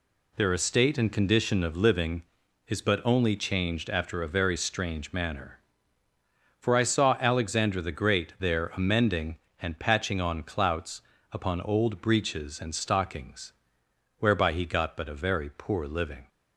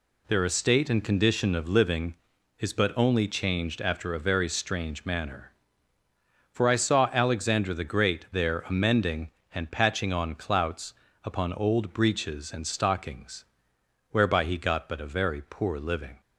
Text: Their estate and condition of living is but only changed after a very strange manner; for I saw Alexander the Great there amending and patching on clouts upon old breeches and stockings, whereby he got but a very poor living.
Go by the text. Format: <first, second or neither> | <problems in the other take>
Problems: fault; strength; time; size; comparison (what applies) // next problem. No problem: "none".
neither | pauses between "clouts" and "upon"; slight; the same in both